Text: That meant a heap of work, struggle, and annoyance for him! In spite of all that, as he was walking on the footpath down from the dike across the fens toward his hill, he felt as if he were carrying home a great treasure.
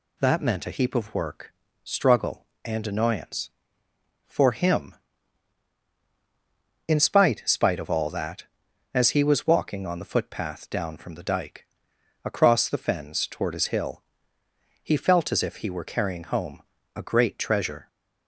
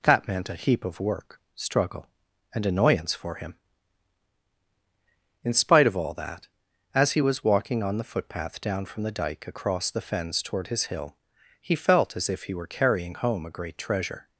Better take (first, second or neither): second